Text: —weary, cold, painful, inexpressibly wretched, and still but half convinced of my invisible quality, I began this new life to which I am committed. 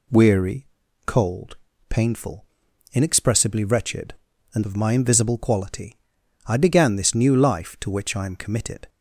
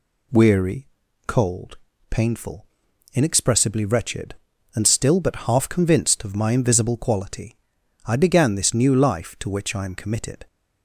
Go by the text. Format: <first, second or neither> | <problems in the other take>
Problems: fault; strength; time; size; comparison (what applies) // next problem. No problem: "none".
second | skips "still but half convinced"; at 4.6 s